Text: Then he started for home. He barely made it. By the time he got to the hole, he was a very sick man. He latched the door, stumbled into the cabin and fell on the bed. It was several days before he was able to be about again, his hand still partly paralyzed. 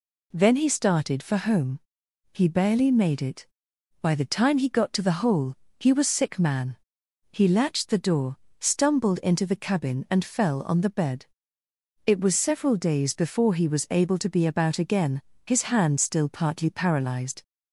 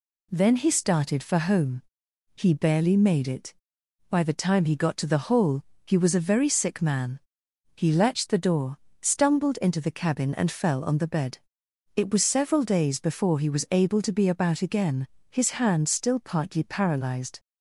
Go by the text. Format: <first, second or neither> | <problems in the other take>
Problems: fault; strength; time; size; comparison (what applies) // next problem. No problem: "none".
second | skips "a very"; at 6.0 s